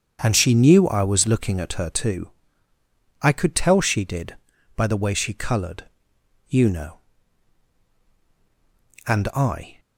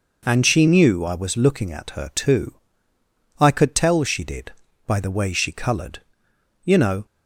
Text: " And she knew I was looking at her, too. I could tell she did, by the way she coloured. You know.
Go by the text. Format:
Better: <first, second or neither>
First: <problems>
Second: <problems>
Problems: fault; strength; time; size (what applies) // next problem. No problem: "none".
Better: second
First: starts louder than the rest; strong; until 1.2 s; 7 dB // goes on to say "And I"; noticeable; from 9.0 s on; 0.73 s long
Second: none